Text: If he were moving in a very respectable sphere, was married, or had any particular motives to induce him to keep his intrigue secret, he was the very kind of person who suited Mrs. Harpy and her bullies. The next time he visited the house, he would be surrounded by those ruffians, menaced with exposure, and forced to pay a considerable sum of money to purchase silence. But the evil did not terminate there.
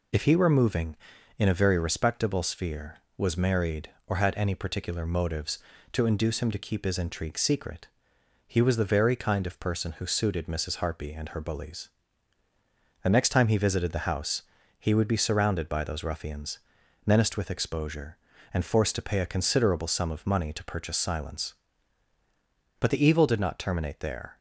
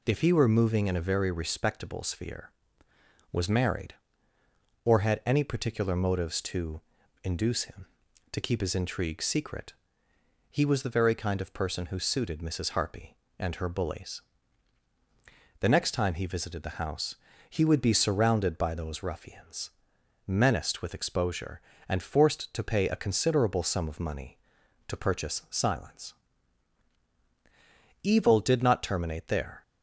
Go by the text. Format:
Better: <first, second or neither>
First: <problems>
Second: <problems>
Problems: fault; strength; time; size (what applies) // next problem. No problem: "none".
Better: first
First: none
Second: pauses between "to" and "induce"; at 6.7 s; 0.42 s long // skips "But the"; at 27.0 s